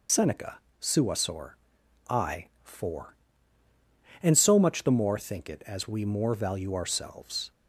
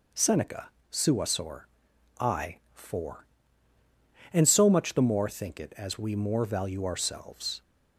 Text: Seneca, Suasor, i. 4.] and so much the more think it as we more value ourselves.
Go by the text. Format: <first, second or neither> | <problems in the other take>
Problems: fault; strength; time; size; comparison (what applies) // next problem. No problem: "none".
second | loses the start of "Seneca"; at 0.0 s; 70 ms